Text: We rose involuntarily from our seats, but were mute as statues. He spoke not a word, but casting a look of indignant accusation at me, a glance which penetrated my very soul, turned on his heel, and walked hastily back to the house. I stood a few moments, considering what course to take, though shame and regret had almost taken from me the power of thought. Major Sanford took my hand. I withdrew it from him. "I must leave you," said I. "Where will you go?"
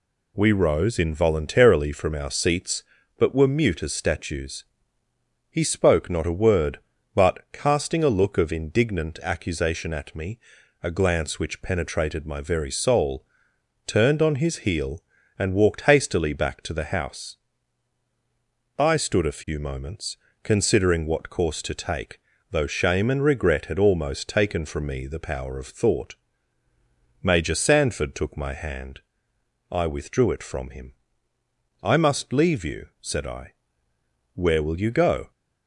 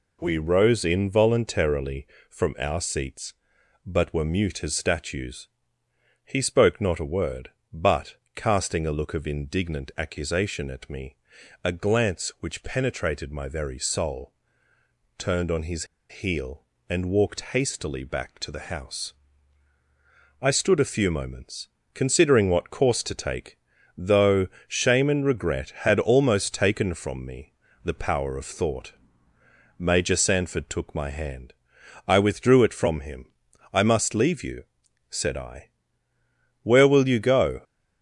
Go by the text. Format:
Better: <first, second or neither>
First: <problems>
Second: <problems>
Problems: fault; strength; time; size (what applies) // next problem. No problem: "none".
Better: first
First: none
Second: pauses between "but" and "casting"; slight; at 8.1 s; 0.18 s long // pauses between "his" and "heel"; slight; at 15.8 s; 0.24 s long // pauses between "though" and "shame"; slight; at 24.4 s; 0.20 s long // pauses between "me" and "the"; slight; at 27.5 s; 0.30 s long